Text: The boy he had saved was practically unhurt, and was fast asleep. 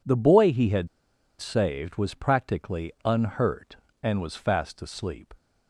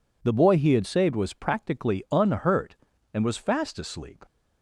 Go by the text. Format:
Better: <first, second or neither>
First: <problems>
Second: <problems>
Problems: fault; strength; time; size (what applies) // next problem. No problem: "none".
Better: second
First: pauses between "had" and "saved"; noticeable; at 0.8 s; 0.52 s long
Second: none